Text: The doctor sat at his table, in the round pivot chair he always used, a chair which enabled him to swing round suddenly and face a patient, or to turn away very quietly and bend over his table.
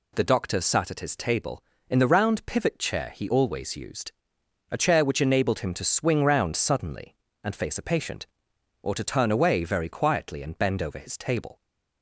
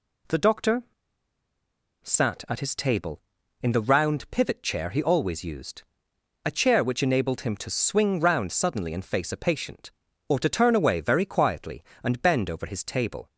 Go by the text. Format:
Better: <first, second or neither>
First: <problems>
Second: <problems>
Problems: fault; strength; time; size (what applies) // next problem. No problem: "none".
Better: first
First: none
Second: pauses between "doctor" and "sat"; at 0.8 s; 1.2 s long